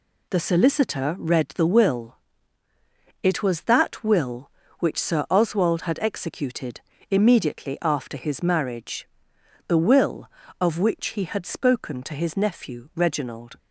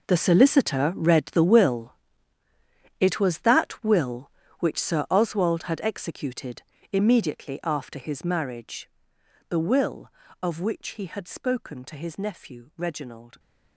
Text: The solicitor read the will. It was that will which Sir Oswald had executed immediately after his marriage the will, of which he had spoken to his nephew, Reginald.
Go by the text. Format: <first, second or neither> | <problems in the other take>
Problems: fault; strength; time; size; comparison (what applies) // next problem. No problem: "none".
first | gets quieter; strong; throughout; 14.5 dB // pauses between "executed" and "immediately"; slight; at 6.6 s; 0.30 s long; slight in the first // pauses between "marriage" and "the"; noticeable; at 8.8 s; 0.60 s long; noticeable in the first